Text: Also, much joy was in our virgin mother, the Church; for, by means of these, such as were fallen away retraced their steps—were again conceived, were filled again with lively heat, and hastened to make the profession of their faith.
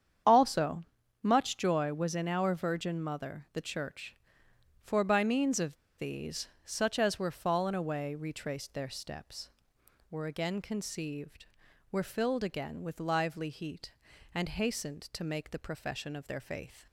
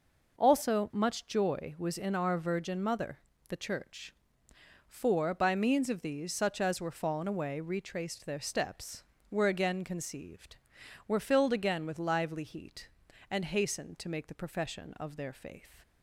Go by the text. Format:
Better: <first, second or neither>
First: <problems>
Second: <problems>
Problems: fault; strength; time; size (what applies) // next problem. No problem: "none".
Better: second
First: starts louder than the rest; strong; until 1.6 s; 8.5 dB // pauses between "of" and "these"; slight; at 5.7 s; 0.22 s long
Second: none